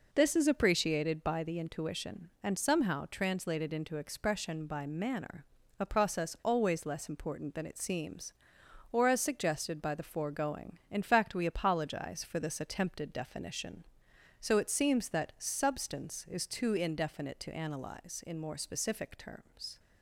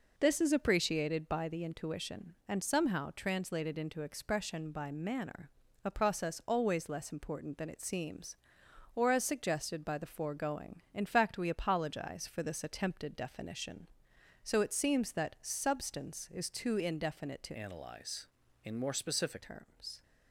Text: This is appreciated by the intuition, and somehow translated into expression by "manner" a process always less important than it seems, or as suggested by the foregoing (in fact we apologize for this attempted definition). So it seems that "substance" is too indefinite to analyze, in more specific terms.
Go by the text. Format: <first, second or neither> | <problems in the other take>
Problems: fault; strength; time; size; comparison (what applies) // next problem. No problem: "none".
first | pauses between "manner" and "a"; slight; at 5.5 s; 0.34 s long; slight in the first // changes voice from "analyze" to "specific"; from 17.5 to 19.4 s; 1.9 s long